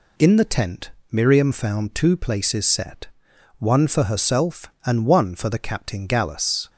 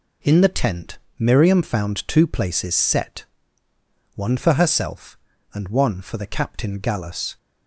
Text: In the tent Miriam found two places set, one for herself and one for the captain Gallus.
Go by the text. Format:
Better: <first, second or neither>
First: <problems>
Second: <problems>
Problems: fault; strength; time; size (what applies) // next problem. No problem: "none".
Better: neither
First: pauses between "tent" and "Miriam"; slight; at 0.9 s; 0.20 s long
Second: pauses between "tent" and "Miriam"; slight; at 0.9 s; 0.18 s long